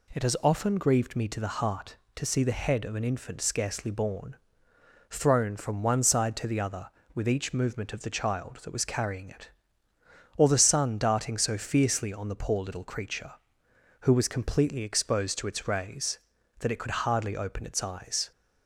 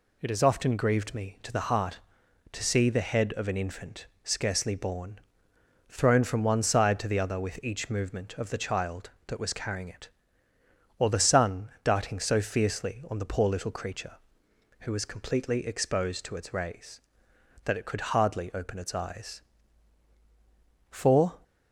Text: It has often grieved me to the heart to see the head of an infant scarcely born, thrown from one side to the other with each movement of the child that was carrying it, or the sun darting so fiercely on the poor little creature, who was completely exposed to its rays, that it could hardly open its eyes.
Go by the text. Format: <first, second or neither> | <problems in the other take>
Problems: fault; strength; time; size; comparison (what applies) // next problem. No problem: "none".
first | pauses between "infant" and "scarcely"; slight; at 4.0 s; 0.16 s long // goes on to say "For"; slight; from 20.8 s on; 0.48 s long